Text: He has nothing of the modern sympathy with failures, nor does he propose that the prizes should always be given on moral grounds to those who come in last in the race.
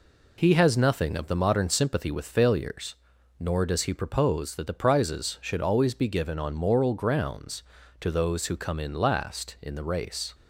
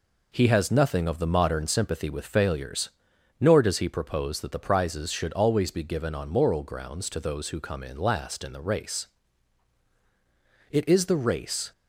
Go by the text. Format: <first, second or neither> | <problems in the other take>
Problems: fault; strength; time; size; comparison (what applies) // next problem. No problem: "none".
first | goes on to say "It is the race"; noticeable; from 10.7 s on; 1.0 s long